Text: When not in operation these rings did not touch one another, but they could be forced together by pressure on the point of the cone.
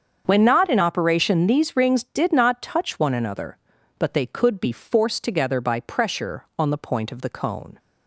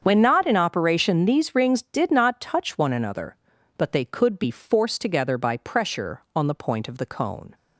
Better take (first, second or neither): neither